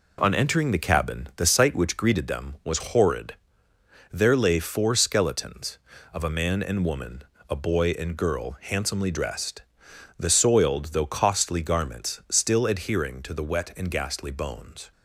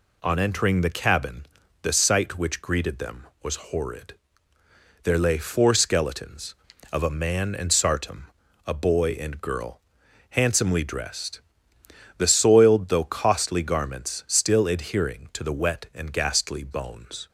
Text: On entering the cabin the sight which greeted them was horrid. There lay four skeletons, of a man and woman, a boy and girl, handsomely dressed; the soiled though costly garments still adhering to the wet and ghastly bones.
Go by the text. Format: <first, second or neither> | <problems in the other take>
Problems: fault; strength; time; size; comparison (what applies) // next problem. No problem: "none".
first | pauses between "cabin" and "the"; slight; at 1.4 s; 0.34 s long // says "sartum" for "woman"; at 7.7 s